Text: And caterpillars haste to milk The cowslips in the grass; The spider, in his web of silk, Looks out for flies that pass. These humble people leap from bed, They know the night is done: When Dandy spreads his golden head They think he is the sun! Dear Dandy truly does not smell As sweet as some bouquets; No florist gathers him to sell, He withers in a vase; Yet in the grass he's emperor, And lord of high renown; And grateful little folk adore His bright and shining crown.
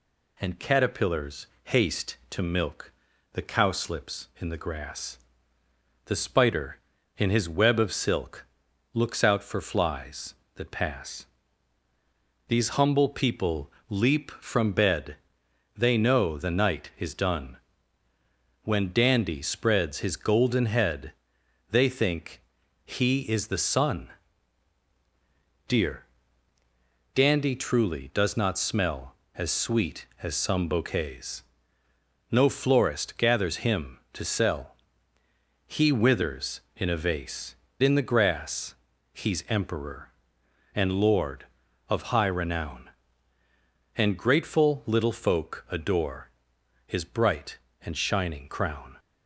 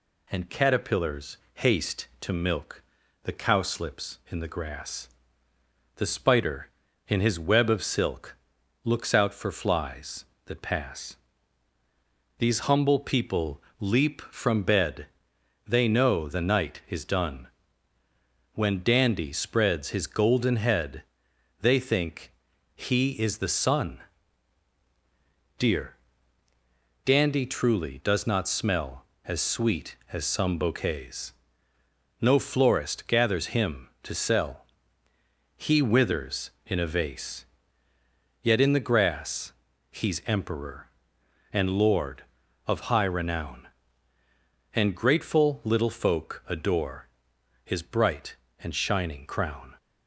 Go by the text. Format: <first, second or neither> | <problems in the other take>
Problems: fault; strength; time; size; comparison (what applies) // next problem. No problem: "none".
second | pauses between "caterpillars" and "haste"; slight; at 1.4 s; 0.18 s long; slight in the second // pauses between "milk" and "The"; at 2.9 s; 0.42 s long; also in the second // pauses between "people" and "leap"; slight; at 13.7 s; 0.16 s long; slight in the second // pauses between "head" and "They"; noticeable; at 21.1 s; 0.58 s long; noticeable in the second // pauses between "think" and "he"; noticeable; at 22.3 s; 0.46 s long; noticeable in the second // pauses between "Dear" and "Dandy"; at 26.0 s; 1.1 s long; also in the second // skips "Yet"; at 37.6 s // pauses between "grass" and "he's"; at 38.7 s; 0.40 s long; also in the second // pauses between "adore" and "His"; noticeable; at 46.2 s; 0.56 s long; noticeable in the second